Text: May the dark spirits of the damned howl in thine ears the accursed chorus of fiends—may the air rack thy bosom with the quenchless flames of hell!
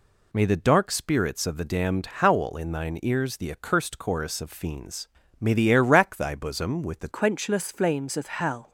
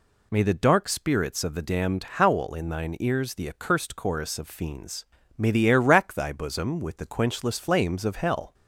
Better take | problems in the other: second | changes voice at "quenchless"; from 7.1 s on; 1.6 s long

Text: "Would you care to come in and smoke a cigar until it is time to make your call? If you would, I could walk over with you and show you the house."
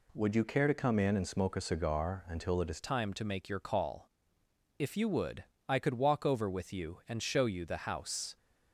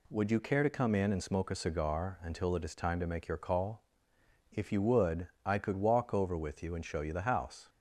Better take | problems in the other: second | changes voice at "time"; from 2.8 s on; 5.5 s long

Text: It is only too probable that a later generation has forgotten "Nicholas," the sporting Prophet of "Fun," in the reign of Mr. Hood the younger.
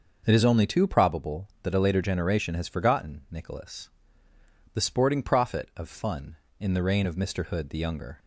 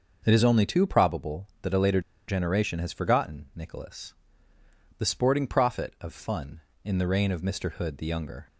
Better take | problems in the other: first | starts louder than the rest; noticeable; until 1.2 s; 6 dB; noticeable in the first // pauses between "later" and "generation"; slight; at 1.9 s; 0.28 s long

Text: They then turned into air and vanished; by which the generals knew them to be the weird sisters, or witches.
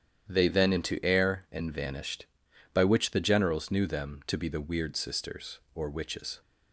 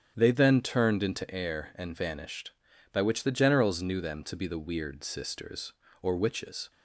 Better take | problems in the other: second | starts louder than the rest; strong; until 1.3 s; 9.5 dB; strong in the second // skips "turned"; at 0.7 s

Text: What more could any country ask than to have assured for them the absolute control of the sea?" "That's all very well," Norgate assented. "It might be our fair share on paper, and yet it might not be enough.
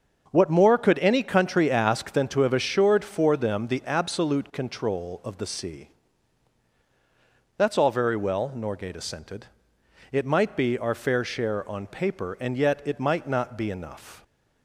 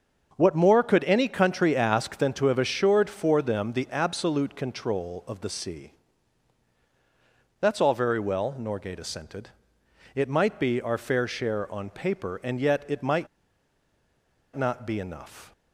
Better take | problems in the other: first | starts louder than the rest; until 1.3 s; 6.5 dB; also in the first // pauses between "might" and "not"; strong; at 13.2 s; 1.2 s long

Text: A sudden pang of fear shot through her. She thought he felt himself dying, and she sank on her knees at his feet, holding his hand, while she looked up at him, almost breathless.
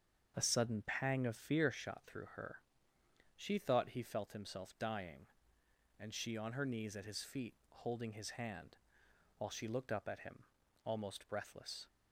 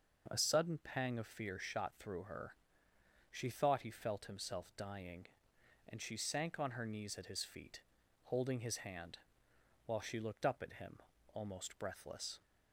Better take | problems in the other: second | starts louder than the rest; strong; until 1.3 s; 7 dB // skips "sank"; at 6.3 s

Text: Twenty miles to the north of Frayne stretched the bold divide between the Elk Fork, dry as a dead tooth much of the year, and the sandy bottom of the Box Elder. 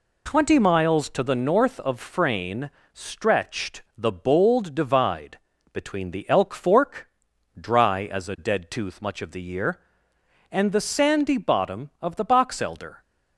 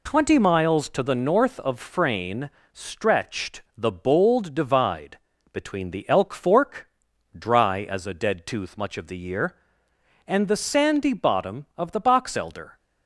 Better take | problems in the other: neither | pauses between "Frayne" and "stretched"; slight; the same in both // pauses between "divide" and "between"; slight; the same in both

